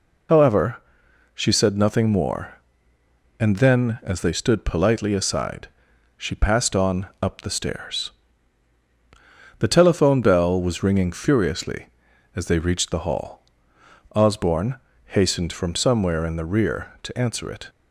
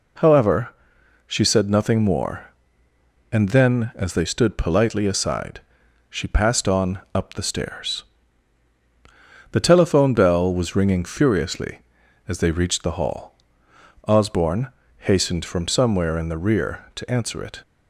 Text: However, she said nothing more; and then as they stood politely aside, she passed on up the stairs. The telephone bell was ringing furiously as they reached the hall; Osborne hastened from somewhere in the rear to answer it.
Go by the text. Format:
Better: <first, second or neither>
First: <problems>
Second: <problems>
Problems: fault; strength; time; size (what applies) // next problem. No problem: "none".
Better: second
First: loses the start of "However"; at 0.2 s; 50 ms // pauses between "Osborne" and "hastened"; slight; at 14.7 s; 0.32 s long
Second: pauses between "Osborne" and "hastened"; slight; at 14.6 s; 0.32 s long